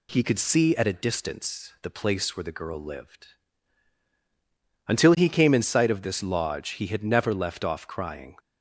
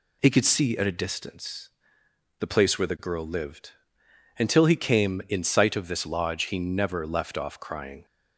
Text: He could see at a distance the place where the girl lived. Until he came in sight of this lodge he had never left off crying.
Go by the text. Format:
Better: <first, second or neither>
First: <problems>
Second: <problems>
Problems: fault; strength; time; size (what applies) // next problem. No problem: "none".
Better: first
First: none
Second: pauses between "distance" and "the"; noticeable; at 1.6 s; 0.70 s long // skips "had"; at 6.5 s